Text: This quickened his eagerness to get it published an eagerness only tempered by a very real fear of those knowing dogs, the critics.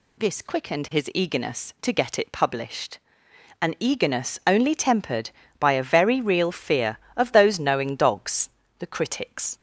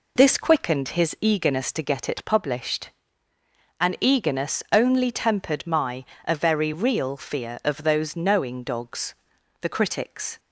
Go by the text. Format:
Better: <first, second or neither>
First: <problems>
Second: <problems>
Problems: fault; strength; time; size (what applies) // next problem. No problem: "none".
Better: first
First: pauses between "published" and "an"; noticeable; at 2.9 s; 0.64 s long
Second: pauses between "published" and "an"; noticeable; at 2.8 s; 0.92 s long // says "my" for "by"; at 5.6 s